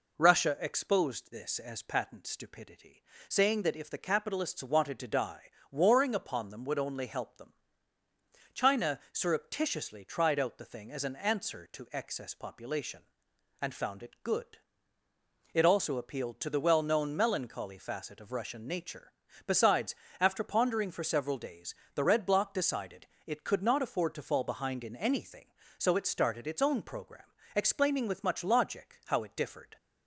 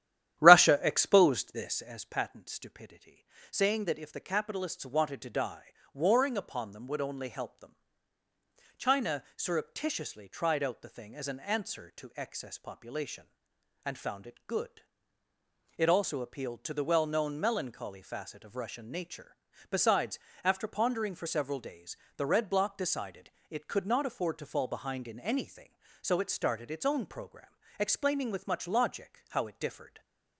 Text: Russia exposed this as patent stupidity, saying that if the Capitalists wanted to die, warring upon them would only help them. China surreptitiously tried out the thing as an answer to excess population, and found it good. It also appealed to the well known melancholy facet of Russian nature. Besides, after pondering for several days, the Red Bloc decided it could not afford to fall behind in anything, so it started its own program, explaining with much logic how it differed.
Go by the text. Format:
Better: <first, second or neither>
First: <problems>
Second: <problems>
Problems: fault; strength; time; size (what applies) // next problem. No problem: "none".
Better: first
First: pauses between "decided" and "it"; slight; at 23.0 s; 0.20 s long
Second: starts louder than the rest; strong; until 1.8 s; 11.5 dB // pauses between "decided" and "it"; slight; at 23.2 s; 0.20 s long